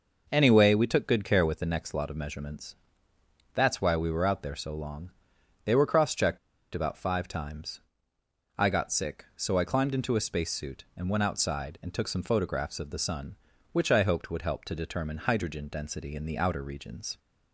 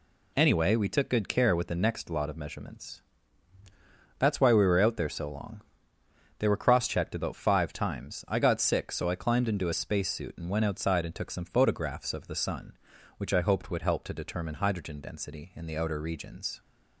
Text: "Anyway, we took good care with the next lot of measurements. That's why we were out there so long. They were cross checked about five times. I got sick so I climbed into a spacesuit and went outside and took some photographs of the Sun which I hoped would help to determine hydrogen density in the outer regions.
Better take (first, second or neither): second